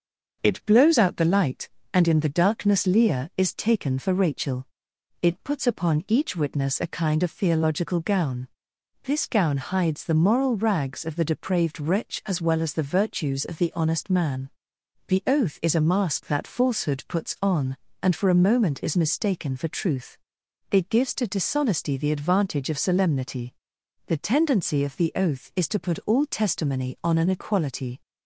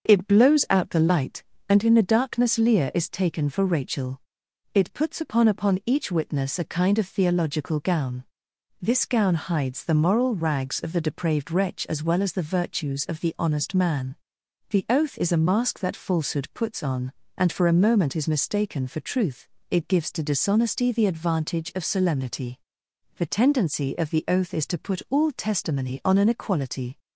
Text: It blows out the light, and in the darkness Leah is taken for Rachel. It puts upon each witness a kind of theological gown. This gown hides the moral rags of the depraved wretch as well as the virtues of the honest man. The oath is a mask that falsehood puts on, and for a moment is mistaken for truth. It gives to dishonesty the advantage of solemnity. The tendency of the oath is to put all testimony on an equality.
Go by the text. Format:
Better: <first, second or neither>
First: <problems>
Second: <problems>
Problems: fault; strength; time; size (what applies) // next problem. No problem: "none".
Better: first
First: starts louder than the rest; until 1.4 s; 6.5 dB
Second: starts louder than the rest; until 1.1 s; 6.5 dB // says "upon" twice; at 5.4 s